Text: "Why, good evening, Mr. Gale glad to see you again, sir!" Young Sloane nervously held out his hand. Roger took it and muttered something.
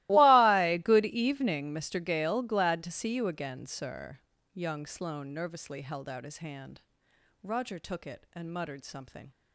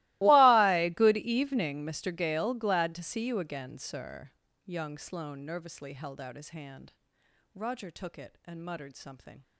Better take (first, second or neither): first